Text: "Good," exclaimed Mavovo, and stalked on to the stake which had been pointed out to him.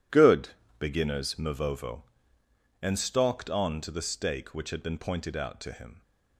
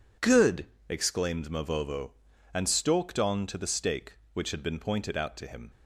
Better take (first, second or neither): second